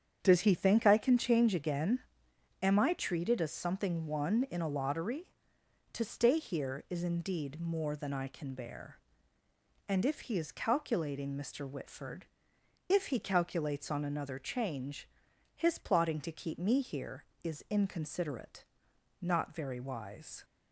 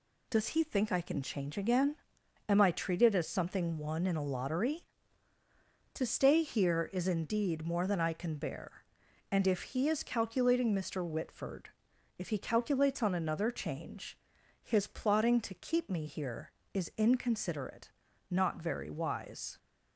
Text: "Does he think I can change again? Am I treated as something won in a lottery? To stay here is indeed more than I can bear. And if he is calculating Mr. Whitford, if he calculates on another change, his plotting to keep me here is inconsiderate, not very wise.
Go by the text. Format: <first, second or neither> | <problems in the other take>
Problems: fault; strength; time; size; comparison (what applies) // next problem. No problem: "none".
second | starts louder than the rest; strong; until 1.4 s; 8 dB